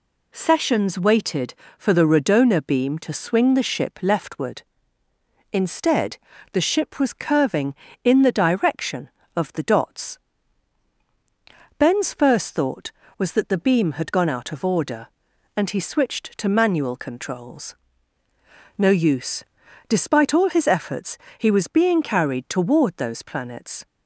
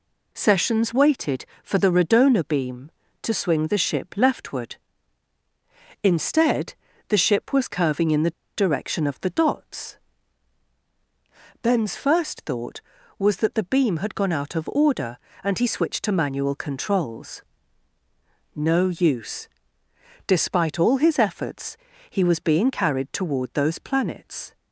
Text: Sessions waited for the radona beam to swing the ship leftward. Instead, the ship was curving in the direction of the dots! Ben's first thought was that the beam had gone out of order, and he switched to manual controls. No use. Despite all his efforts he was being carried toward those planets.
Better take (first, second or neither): first